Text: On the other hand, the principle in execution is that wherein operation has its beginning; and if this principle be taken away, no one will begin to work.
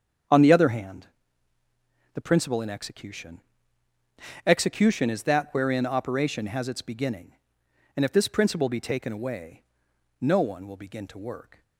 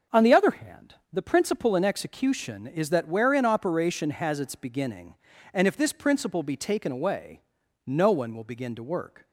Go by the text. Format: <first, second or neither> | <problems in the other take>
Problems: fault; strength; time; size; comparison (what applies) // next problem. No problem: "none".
second | starts louder than the rest; strong; until 2.3 s; 8 dB // says "execution" twice; at 4.4 s